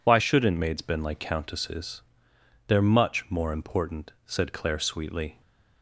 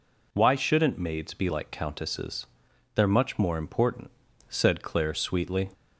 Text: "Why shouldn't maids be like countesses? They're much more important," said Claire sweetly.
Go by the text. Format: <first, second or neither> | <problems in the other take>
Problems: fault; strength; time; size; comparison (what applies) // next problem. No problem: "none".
second | says "been" for "be"; at 0.8 s